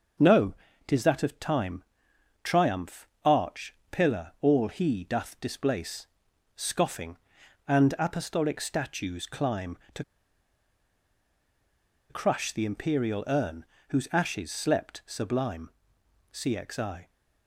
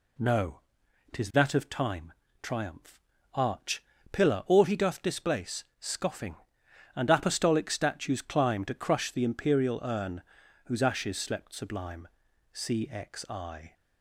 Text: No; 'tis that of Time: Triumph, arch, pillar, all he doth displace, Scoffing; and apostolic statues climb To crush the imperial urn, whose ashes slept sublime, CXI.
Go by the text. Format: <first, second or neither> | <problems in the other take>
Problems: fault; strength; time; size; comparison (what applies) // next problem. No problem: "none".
second | starts louder than the rest; until 1.5 s; 6.5 dB // pauses between "To" and "crush"; strong; at 10.0 s; 2.0 s long